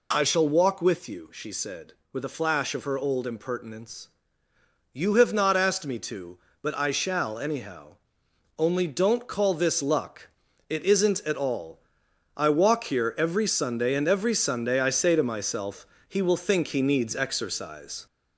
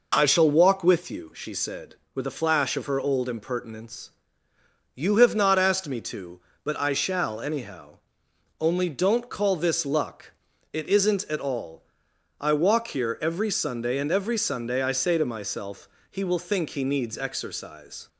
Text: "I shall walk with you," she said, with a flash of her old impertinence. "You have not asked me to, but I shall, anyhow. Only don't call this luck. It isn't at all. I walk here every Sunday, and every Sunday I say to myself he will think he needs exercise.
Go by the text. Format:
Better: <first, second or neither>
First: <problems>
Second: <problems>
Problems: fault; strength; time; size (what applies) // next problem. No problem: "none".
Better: second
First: gets louder; throughout; 3.5 dB // pauses between "myself" and "he"; slight; at 15.8 s; 0.22 s long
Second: pauses between "myself" and "he"; slight; at 15.8 s; 0.22 s long